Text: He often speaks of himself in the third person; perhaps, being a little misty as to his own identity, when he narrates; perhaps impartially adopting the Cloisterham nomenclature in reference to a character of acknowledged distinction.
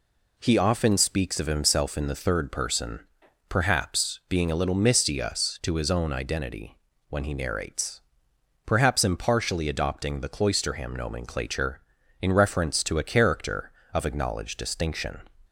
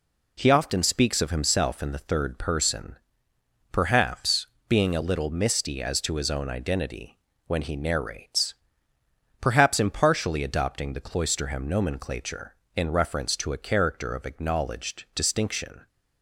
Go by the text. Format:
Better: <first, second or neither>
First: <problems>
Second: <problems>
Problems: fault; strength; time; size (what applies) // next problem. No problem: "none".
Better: second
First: says "us" for "as"; at 5.1 s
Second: none